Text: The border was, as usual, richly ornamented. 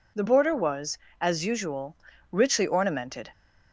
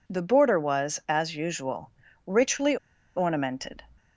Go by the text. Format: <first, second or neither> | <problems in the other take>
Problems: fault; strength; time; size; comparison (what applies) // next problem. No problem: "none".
first | pauses between "richly" and "ornamented"; at 2.7 s; 0.40 s long